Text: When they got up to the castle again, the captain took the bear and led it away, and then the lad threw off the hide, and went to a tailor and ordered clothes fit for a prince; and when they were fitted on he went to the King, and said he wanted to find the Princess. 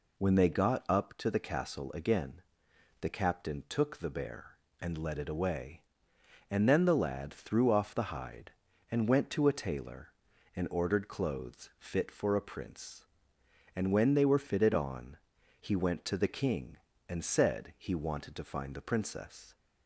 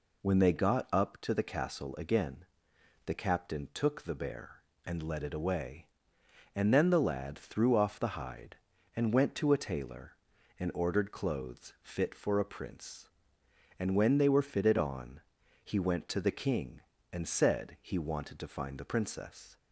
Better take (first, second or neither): neither